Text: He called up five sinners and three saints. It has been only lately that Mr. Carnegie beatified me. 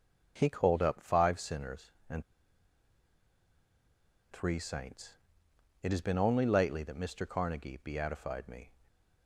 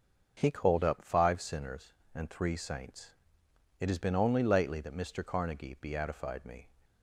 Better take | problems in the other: second | starts louder than the rest; until 1.3 s; 6.5 dB; also in the second // pauses between "and" and "three"; strong; at 2.2 s; 2.0 s long

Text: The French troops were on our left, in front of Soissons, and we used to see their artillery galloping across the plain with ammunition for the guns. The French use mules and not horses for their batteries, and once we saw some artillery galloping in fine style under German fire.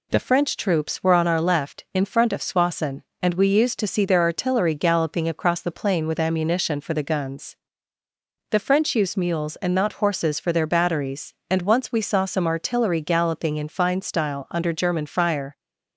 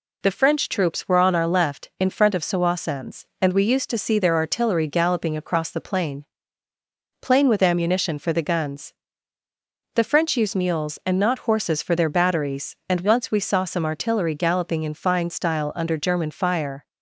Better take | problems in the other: first | says "plain" twice; at 7.1 s

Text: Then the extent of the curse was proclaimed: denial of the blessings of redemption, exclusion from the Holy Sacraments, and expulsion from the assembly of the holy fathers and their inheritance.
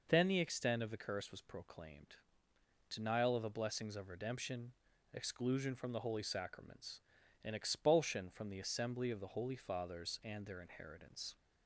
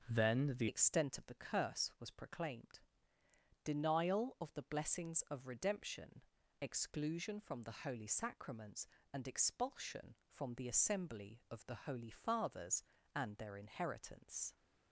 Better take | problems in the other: first | starts louder than the rest; until 1.1 s; 6 dB // changes voice at "extent"; from 0.6 s on; 13.9 s long

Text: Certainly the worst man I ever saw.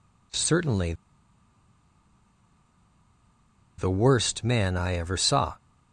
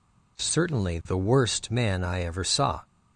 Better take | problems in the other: second | pauses between "Certainly" and "the"; strong; at 0.9 s; 2.8 s long

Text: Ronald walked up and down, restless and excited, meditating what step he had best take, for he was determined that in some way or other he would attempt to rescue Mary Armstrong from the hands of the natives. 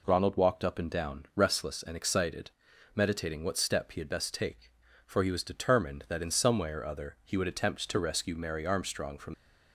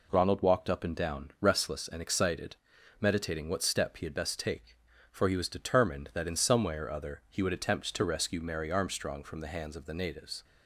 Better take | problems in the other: second | stops before "the hands of the natives"; at 9.3 s

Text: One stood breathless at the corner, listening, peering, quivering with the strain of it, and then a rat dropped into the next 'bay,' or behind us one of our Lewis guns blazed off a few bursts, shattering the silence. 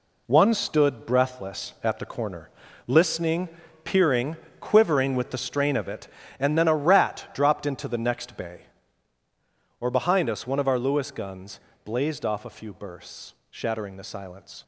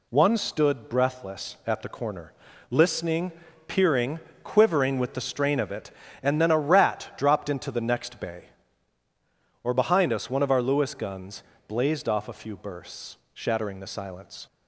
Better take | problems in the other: second | gets quieter; strong; throughout; 8.5 dB // pauses between "guns" and "blazed"; slight; at 11.5 s; 0.24 s long; slight in the second

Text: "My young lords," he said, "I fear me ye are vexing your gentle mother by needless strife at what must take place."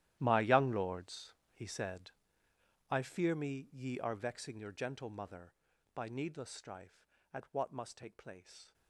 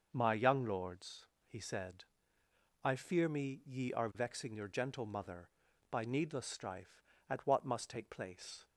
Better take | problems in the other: second | gets quieter; strong; throughout; 16.5 dB // starts louder than the rest; strong; until 1.2 s; 13 dB; noticeable in the second

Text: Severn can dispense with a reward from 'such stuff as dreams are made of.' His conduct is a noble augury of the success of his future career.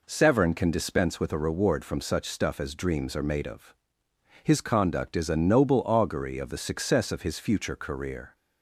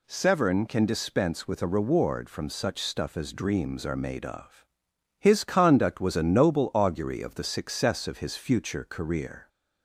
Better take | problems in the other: first | says "was" for "is"; at 5.9 s

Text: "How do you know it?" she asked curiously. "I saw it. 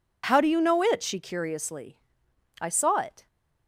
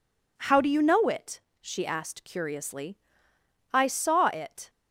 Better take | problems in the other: second | skips "asked"; at 1.1 s

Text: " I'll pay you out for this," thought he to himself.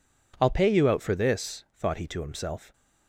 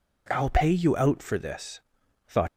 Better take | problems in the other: first | stops before "he to himself"; at 2.4 s

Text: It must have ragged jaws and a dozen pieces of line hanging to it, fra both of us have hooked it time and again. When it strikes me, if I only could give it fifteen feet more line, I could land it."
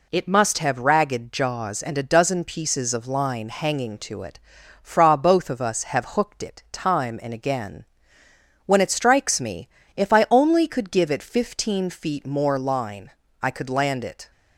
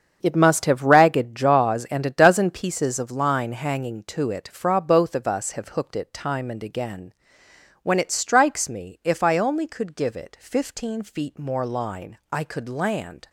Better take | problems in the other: first | starts louder than the rest; strong; until 1.2 s; 7.5 dB // stops before "it"; at 13.2 s

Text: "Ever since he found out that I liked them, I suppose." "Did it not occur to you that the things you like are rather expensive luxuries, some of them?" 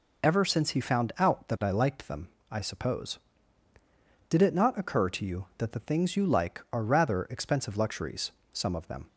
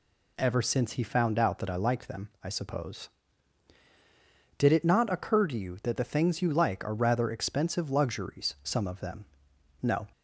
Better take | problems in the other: first | goes on to say "No"; slight; from 9.8 s on; 0.24 s long

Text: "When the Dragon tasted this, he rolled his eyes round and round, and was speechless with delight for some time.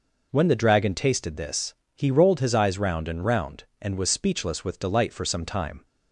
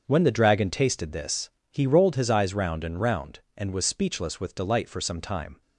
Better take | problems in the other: first | gets quieter; strong; throughout; 11.5 dB

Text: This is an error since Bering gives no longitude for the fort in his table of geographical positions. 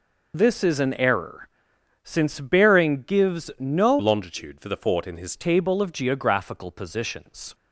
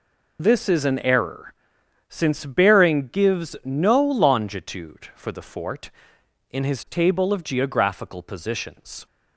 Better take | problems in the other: second | pauses between "error" and "since"; noticeable; at 1.4 s; 0.56 s long; noticeable in the second // changes voice from "longitude" to "his"; from 3.9 to 5.3 s; 1.4 s long

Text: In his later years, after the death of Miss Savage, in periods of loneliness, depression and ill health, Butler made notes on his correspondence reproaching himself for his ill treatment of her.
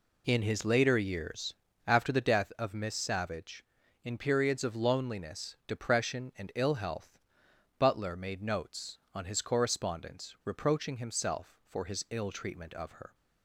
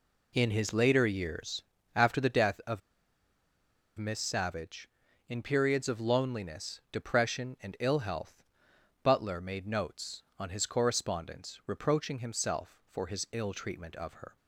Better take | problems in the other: first | pauses between "of" and "Miss"; at 2.8 s; 1.1 s long

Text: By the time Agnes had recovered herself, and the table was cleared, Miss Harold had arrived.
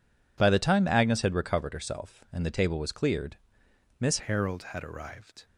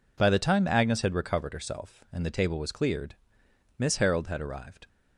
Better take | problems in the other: second | changes voice at "Harold"; from 4.1 s on; 1.3 s long

